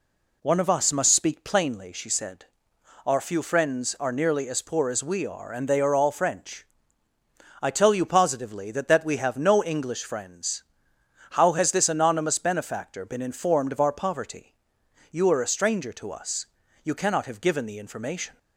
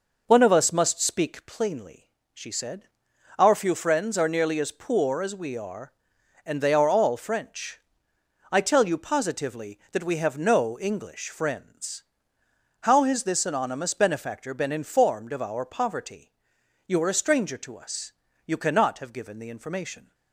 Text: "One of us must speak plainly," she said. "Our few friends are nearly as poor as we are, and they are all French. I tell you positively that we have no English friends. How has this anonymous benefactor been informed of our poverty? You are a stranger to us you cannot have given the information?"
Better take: second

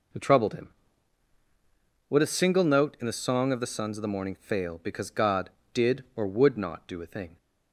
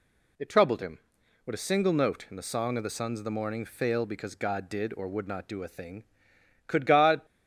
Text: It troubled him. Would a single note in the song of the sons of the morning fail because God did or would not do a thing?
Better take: first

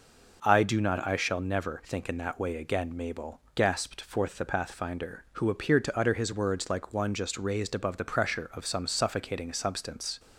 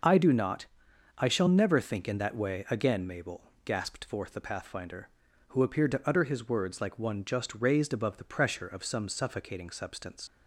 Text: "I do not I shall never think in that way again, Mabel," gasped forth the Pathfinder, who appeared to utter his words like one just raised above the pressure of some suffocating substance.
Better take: first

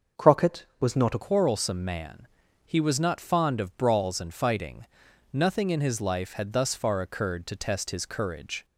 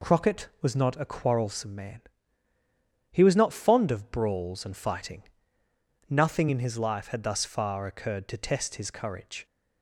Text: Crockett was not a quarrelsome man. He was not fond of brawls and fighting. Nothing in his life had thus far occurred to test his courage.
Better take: second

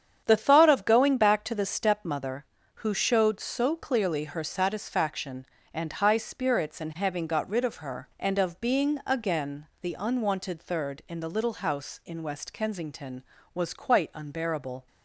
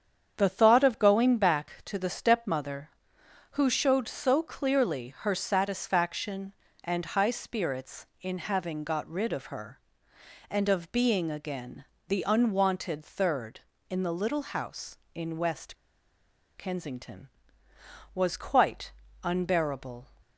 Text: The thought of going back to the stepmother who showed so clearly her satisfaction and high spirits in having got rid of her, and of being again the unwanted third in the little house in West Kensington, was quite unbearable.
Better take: first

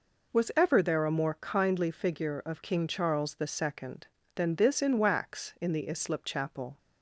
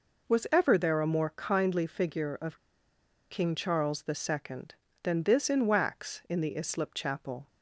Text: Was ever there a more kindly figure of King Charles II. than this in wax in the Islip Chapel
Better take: first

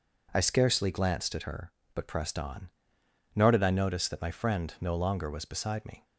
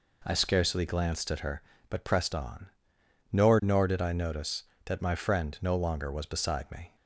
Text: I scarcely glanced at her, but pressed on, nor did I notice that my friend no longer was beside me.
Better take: first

